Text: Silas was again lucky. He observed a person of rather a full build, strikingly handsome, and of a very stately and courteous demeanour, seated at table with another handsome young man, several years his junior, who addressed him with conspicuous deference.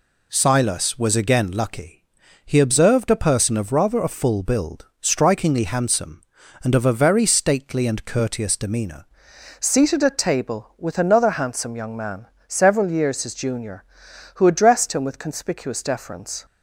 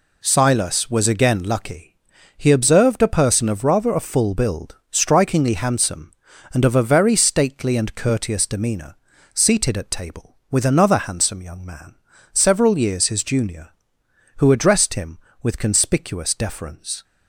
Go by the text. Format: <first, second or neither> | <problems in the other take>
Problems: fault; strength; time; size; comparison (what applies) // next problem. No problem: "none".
second | changes voice at "seated"; from 9.5 s on; 6.9 s long